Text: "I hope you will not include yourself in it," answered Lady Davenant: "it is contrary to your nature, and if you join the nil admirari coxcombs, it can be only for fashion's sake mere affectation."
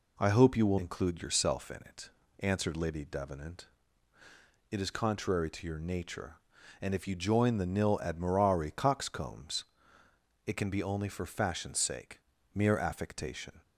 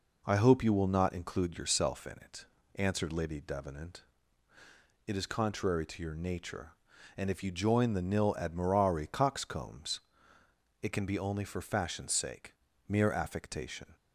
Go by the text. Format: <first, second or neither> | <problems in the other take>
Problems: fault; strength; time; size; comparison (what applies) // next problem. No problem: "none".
second | skips "not"; at 0.7 s // pauses between "sake" and "mere"; slight; at 12.1 s; 0.34 s long; slight in the second